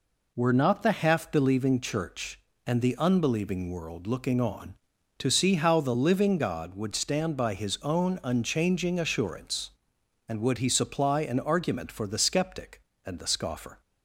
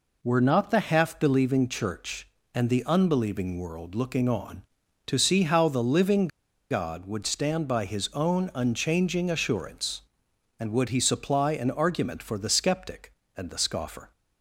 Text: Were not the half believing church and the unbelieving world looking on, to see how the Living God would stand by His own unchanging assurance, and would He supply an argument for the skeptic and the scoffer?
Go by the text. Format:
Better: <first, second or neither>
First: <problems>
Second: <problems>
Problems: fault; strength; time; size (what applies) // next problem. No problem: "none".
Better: first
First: none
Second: pauses between "Living" and "God"; at 6.2 s; 0.43 s long